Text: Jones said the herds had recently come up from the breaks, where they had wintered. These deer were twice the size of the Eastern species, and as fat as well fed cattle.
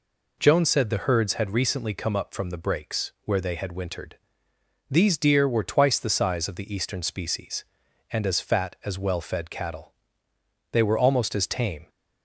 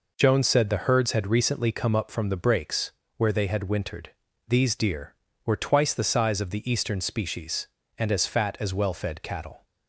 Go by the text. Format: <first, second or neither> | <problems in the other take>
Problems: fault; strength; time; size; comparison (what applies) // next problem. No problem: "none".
second | goes on to say "They were almost as tame"; noticeable; from 10.7 s on; 1.1 s long